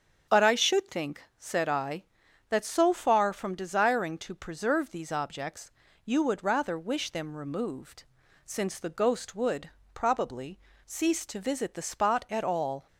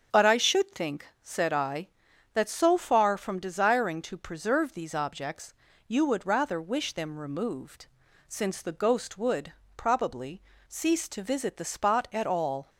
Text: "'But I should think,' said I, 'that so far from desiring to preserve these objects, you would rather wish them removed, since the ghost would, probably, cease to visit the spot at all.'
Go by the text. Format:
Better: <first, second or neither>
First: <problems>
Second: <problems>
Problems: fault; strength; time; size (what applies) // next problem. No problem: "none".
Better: neither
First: starts louder than the rest; strong; until 1.4 s; 7.5 dB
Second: starts louder than the rest; strong; until 1.2 s; 7.5 dB